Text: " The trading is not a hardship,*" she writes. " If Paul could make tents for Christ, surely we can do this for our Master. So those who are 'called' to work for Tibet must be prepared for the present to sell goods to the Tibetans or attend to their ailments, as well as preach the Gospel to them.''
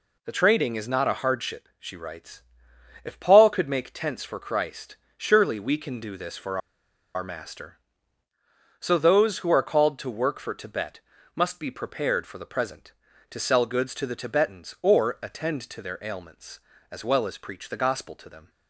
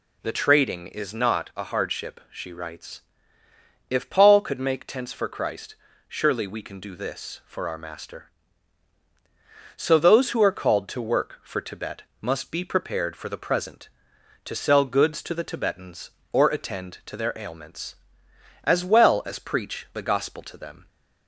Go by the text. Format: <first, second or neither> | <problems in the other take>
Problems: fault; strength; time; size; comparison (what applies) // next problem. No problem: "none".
second | pauses between "for" and "our"; noticeable; at 6.5 s; 0.56 s long // pauses between "Tibet" and "must"; slight; at 10.9 s; 0.36 s long; slight in the second